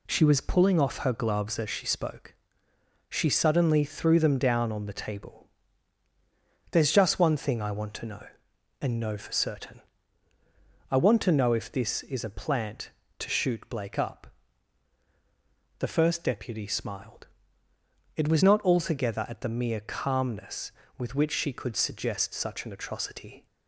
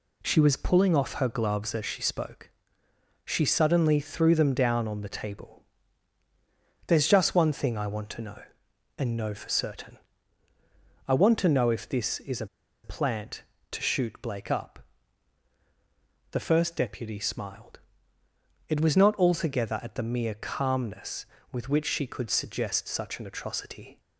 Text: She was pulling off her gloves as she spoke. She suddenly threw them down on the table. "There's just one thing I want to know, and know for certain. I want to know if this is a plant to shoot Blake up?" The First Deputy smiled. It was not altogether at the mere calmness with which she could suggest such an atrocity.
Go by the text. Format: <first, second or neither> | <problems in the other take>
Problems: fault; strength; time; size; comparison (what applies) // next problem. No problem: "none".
first | pauses between "a" and "plant"; at 12.4 s; 0.37 s long